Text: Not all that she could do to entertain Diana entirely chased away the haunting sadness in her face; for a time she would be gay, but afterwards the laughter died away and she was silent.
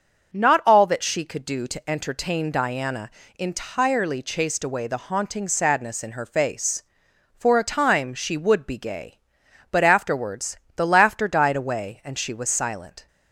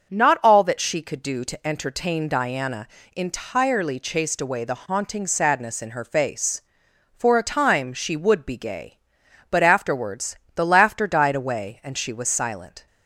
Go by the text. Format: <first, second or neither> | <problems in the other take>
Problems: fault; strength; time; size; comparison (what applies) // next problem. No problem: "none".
neither | starts louder than the rest; the same in both // pauses between "Diana" and "entirely"; slight; the same in both // pauses between "afterwards" and "the"; slight; the same in both